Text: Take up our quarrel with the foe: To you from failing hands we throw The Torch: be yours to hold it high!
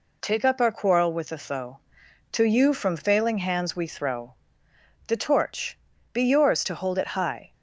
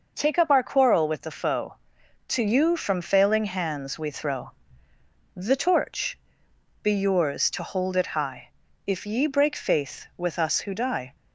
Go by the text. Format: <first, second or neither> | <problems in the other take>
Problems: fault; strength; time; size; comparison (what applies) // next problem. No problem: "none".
first | pauses between "throw" and "The"; noticeable; at 4.5 s; 0.84 s long; noticeable in the first // goes on to say "If ye break faith with us who die"; strong; from 8.8 s on; 2.2 s long